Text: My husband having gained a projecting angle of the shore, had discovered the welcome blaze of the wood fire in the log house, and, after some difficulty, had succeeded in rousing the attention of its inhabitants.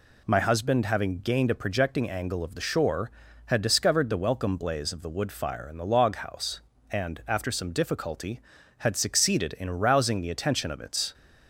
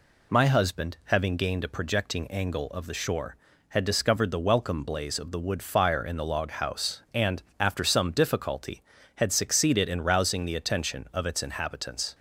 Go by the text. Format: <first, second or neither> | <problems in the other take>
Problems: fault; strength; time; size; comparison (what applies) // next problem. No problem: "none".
second | stops before "inhabitants"; at 11.1 s